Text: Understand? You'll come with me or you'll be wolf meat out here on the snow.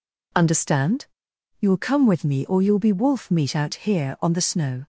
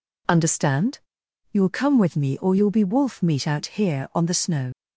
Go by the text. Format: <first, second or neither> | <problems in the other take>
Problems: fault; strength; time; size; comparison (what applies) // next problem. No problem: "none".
first | leaves "snow" unfinished; at 4.7 s; 60 ms